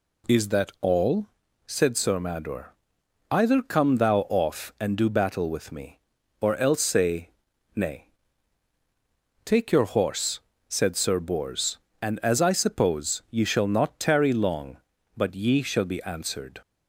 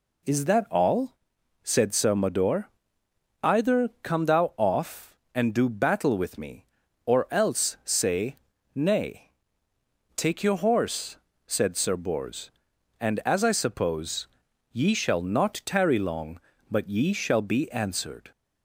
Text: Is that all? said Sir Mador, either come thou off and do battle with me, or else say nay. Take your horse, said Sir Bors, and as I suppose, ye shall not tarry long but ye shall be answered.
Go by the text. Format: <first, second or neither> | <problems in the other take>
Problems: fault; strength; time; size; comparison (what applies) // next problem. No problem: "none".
neither | pauses between "say" and "nay"; the same in both